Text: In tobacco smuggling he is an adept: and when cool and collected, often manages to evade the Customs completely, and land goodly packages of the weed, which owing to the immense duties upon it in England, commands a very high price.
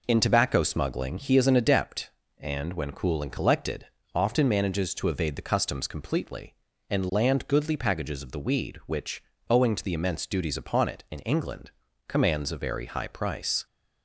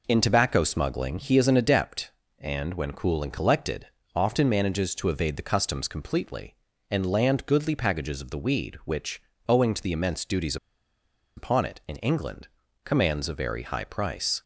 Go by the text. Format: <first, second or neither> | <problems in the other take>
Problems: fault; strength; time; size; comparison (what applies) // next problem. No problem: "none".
first | pauses between "which" and "owing"; slight; at 9.2 s; 0.26 s long; slight in the first // pauses between "duties" and "upon"; noticeable; at 10.5 s; 0.80 s long